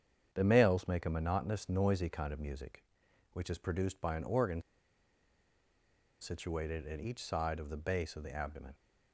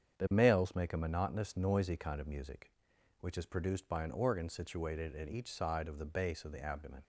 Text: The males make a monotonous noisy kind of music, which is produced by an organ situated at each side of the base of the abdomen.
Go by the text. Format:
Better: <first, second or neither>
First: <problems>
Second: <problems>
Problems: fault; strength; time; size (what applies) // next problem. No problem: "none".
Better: second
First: starts louder than the rest; strong; until 1.3 s; 8 dB // pauses between "organ" and "situated"; strong; at 4.6 s; 1.5 s long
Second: starts louder than the rest; strong; until 1.2 s; 8 dB